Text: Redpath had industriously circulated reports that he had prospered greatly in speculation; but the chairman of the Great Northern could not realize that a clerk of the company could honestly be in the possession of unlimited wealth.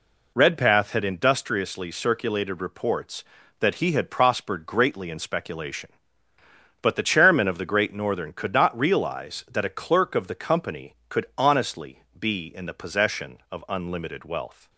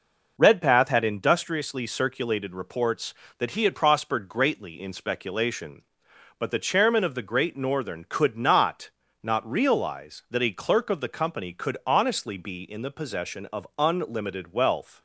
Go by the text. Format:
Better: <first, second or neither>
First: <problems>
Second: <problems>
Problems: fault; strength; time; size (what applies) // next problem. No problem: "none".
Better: first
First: none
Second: says "not" twice; at 9.2 s